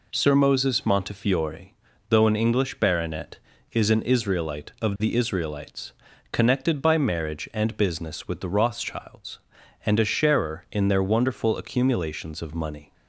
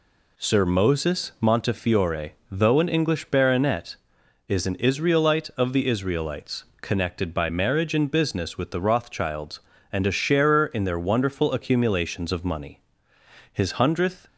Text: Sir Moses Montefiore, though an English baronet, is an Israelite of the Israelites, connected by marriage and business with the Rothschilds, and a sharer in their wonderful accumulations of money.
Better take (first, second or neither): first